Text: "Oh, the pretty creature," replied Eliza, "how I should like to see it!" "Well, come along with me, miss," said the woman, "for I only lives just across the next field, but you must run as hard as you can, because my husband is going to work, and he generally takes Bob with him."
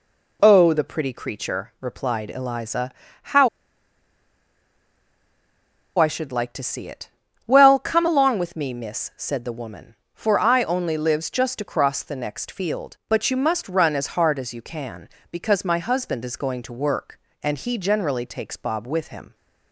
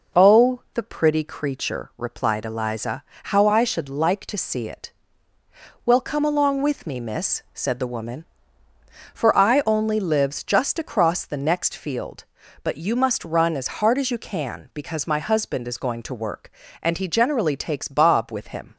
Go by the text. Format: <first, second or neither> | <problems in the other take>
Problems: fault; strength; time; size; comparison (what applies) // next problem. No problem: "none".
second | pauses between "how" and "I"; strong; at 3.4 s; 2.4 s long